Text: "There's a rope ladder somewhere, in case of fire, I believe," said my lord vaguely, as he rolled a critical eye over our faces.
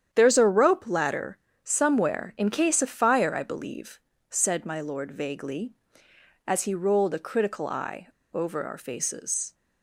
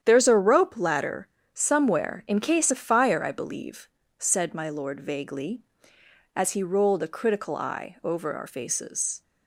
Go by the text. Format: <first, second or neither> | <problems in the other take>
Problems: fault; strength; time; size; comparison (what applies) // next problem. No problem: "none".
second | starts louder than the rest; strong; until 1.1 s; 9 dB; strong in the second // pauses between "ladder" and "somewhere"; slight; at 1.3 s; 0.26 s long; slight in the second // pauses between "eye" and "over"; slight; at 8.0 s; 0.24 s long